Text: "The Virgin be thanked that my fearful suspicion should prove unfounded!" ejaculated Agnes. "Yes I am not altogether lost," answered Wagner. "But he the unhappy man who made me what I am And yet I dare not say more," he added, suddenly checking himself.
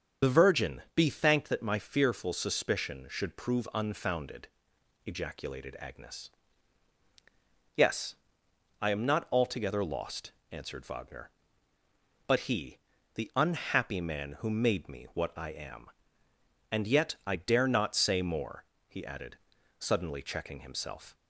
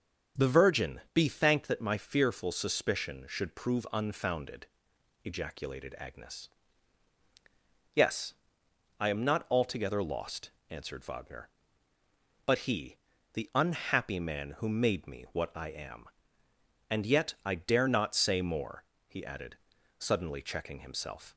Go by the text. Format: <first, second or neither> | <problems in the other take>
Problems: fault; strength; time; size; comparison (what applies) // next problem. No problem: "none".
second | loses the start of "The"; at 0.2 s; 55 ms // starts louder than the rest; until 1.3 s; 7 dB; strong in the second // pauses between "Yes" and "I"; noticeable; at 8.1 s; 0.66 s long; noticeable in the second // pauses between "he" and "the"; slight; at 12.7 s; 0.34 s long; slight in the second